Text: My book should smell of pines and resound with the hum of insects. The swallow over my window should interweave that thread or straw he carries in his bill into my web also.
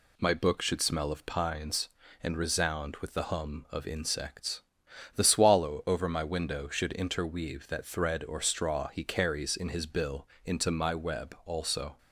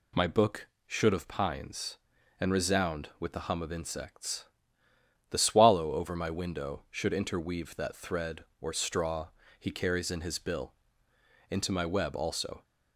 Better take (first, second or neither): first